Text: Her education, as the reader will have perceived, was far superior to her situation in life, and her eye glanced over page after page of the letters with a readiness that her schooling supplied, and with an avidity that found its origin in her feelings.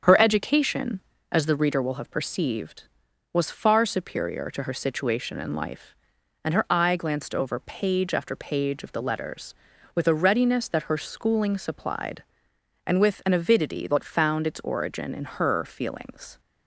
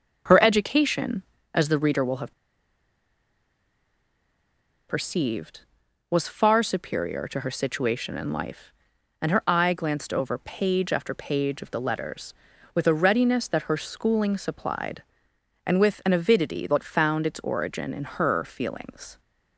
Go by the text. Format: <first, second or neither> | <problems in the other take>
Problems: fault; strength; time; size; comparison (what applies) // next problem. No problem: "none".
first | starts louder than the rest; strong; until 1.5 s; 7.5 dB; strong in the first // pauses between "have" and "perceived"; strong; at 2.3 s; 2.5 s long